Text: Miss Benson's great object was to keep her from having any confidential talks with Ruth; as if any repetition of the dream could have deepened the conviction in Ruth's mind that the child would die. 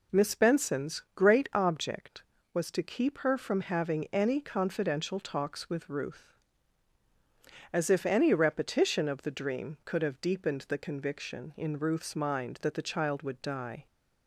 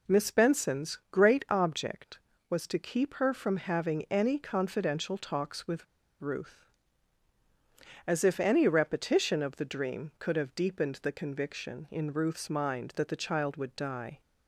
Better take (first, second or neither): first